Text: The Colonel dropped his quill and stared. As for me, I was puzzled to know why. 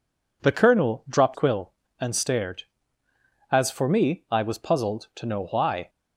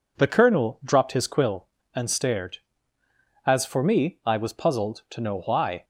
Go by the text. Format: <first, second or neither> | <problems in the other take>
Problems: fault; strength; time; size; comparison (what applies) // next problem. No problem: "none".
second | skips "his"; at 1.3 s